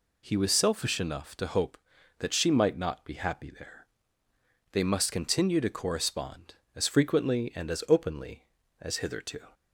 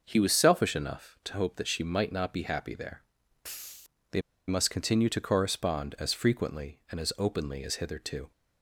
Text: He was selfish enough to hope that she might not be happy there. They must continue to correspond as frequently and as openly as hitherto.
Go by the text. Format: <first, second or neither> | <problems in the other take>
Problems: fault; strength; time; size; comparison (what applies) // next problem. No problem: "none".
first | pauses between "They" and "must"; slight; at 4.2 s; 0.26 s long